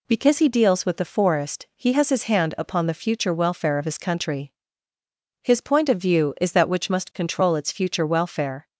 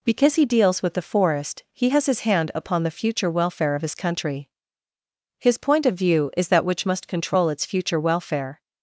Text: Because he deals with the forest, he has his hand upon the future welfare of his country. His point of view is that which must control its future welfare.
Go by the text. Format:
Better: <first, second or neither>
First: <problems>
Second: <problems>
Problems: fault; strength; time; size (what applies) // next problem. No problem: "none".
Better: neither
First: none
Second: none